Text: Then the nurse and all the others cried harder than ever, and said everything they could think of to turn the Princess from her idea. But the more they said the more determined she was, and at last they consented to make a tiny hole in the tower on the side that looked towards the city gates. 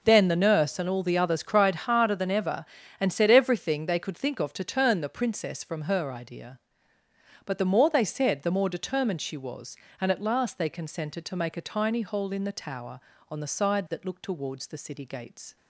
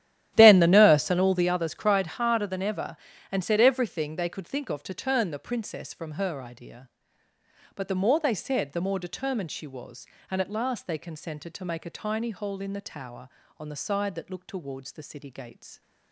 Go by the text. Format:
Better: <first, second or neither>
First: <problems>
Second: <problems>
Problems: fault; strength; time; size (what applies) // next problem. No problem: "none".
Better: first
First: none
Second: starts louder than the rest; strong; until 1.5 s; 12.5 dB